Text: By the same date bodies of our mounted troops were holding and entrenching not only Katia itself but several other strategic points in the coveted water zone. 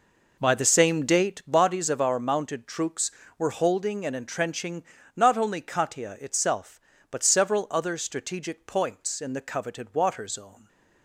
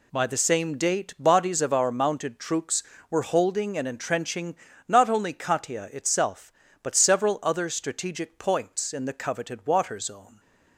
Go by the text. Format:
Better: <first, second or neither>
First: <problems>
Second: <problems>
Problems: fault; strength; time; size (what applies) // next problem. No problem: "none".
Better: second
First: starts louder than the rest; noticeable; until 1.4 s; 4.5 dB // pauses between "entrenching" and "not"; slight; at 4.8 s; 0.32 s long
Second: pauses between "entrenching" and "not"; slight; at 4.5 s; 0.32 s long